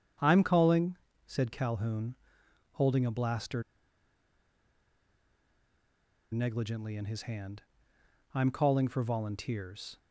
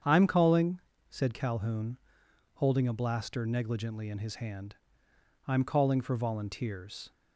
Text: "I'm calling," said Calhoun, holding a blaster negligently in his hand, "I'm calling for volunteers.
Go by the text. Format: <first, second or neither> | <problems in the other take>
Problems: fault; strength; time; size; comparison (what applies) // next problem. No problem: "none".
second | starts louder than the rest; strong; until 1.5 s; 8 dB; strong in the second // pauses between "blaster" and "negligently"; strong; at 3.6 s; 2.6 s long